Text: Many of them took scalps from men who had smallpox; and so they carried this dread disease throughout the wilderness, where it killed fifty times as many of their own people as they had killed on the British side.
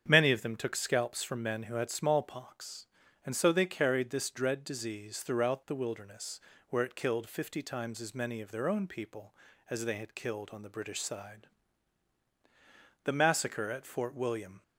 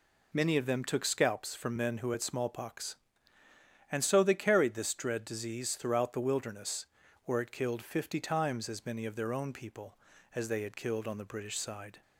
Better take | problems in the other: second | starts louder than the rest; strong; until 1.0 s; 8 dB // goes on to say "The massacre at Fort William"; from 13.0 s on; 1.5 s long

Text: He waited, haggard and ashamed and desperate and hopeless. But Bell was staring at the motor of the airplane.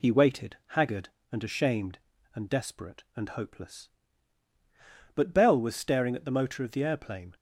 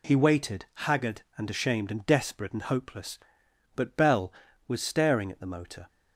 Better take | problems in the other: first | stops before "of the airplane"; at 5.8 s

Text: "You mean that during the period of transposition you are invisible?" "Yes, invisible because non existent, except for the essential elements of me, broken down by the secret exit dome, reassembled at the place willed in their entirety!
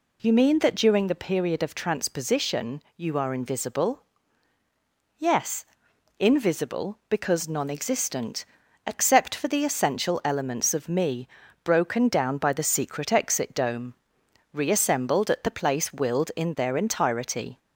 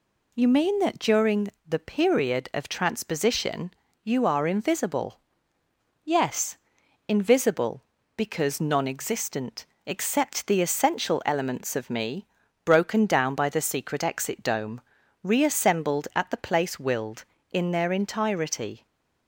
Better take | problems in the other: first | pauses between "during" and "the"; slight; at 1.4 s; 0.18 s long // pauses between "transposition" and "you"; slight; at 3.7 s; 0.32 s long // skips "for"; at 10.4 s // stays silent after the last word; slight; from 18.7 s on; 0.5 s long

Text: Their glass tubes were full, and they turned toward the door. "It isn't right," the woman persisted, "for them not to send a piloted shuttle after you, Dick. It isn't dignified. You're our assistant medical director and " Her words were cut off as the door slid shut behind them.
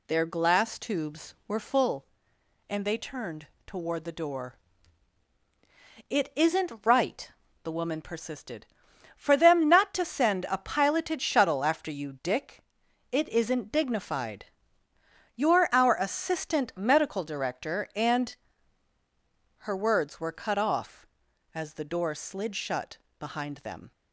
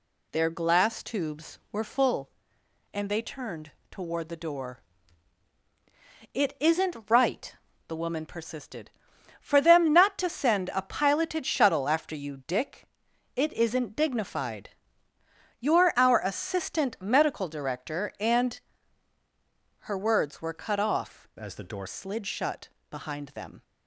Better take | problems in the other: first | pauses between "turned" and "toward"; slight; at 3.7 s; 0.20 s long; slight in the first // changes voice from "as" to "door"; from 21.3 to 21.8 s; 0.5 s long // pauses between "shut" and "behind"; slight; at 22.6 s; 0.22 s long; slight in the first

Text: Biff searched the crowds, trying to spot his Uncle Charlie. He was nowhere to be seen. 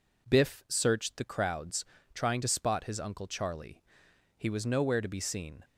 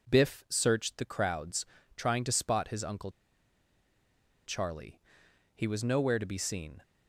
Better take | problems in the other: first | pauses between "Uncle" and "Charlie"; strong; at 3.1 s; 1.3 s long

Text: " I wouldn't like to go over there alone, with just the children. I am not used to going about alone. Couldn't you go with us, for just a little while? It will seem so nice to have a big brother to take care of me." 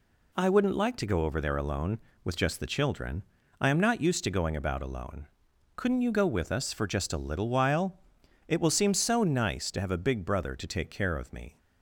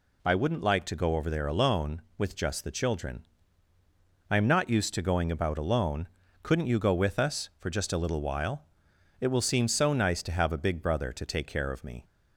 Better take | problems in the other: neither | none

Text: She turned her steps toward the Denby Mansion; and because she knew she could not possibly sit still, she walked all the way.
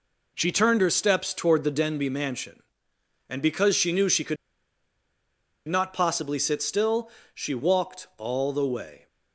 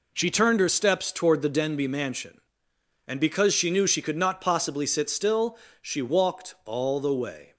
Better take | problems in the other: second | pauses between "could" and "not"; strong; at 4.3 s; 1.3 s long

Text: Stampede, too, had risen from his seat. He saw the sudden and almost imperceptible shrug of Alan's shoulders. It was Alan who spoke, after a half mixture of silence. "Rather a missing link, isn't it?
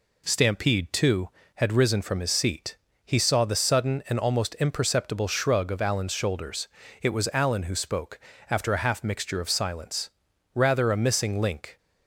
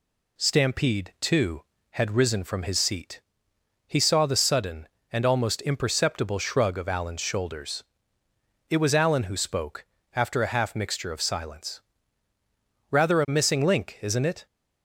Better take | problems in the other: second | stops before "isn't it"; at 11.7 s

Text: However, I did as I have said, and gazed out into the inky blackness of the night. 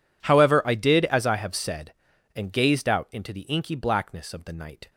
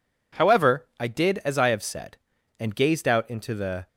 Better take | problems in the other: first | stops before "inky blackness of the night"; at 3.8 s

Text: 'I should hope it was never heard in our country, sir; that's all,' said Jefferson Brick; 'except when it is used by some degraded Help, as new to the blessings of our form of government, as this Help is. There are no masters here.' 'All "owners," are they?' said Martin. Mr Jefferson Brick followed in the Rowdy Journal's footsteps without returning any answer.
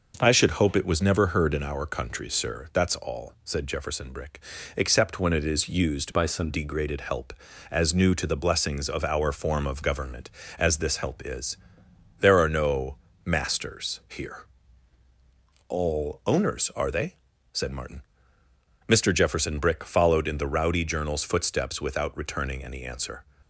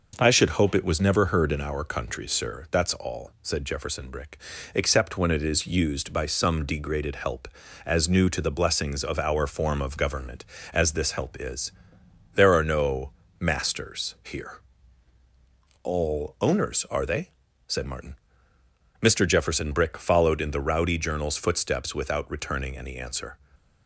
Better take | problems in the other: second | changes voice from "by" to "some"; from 6.1 to 6.4 s; 0.3 s long // pauses between "no" and "masters"; slight; at 12.9 s; 0.30 s long; slight in the second

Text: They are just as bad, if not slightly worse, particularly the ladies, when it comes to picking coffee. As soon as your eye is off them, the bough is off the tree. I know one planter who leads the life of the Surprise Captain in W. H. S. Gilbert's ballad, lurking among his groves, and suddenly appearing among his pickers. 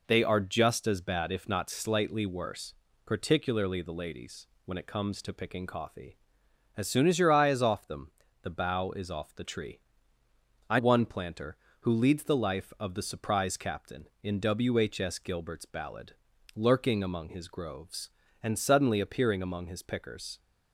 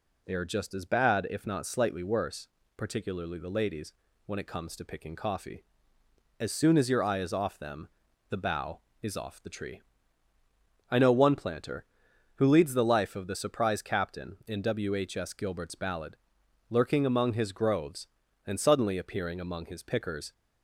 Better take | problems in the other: second | skips "know"; at 10.7 s

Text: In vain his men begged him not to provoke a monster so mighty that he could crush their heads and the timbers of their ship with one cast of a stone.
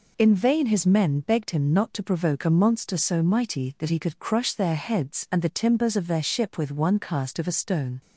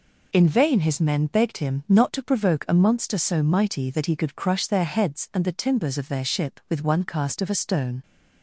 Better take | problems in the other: neither | none

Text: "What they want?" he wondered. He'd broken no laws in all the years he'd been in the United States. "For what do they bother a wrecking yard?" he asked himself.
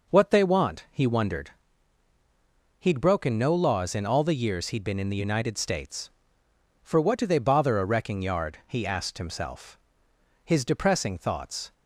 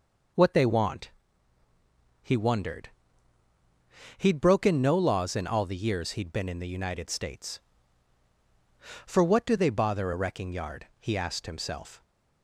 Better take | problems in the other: second | goes on to say "His depressing thoughts"; noticeable; from 10.4 s on; 1.2 s long

